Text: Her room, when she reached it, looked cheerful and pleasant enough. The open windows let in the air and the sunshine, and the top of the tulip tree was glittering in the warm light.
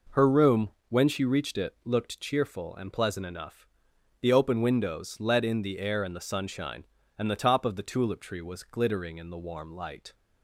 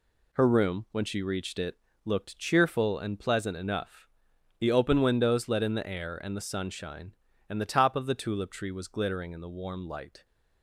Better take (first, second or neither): neither